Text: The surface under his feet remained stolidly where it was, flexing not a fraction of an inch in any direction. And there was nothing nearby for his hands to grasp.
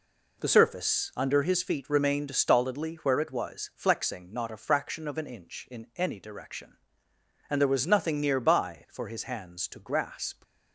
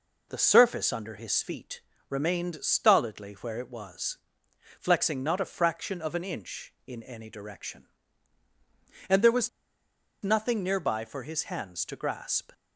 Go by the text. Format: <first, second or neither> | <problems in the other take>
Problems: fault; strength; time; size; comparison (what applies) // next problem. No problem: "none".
first | pauses between "feet" and "remained"; slight; at 1.8 s; 0.26 s long // pauses between "was" and "nothing"; noticeable; at 9.4 s; 0.73 s long